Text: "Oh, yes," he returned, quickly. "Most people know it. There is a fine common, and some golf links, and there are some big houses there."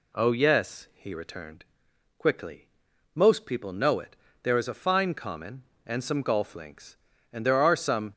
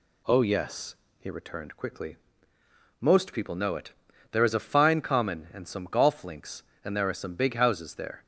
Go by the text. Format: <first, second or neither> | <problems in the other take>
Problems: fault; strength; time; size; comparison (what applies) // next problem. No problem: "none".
second | stops before "big houses there"; at 8.1 s